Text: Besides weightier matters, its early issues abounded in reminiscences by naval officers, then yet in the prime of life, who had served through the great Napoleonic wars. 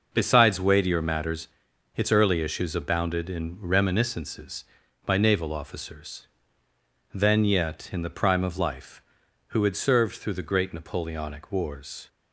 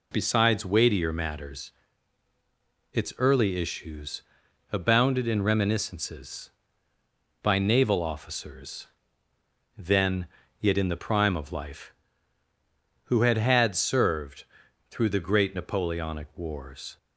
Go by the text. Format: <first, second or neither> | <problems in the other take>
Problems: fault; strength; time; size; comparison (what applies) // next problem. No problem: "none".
first | pauses between "issues" and "abounded"; noticeable; at 4.2 s; 0.50 s long // pauses between "then" and "yet"; slight; at 10.2 s; 0.34 s long // says "had" twice; at 13.3 s // pauses between "served" and "through"; noticeable; at 14.4 s; 0.46 s long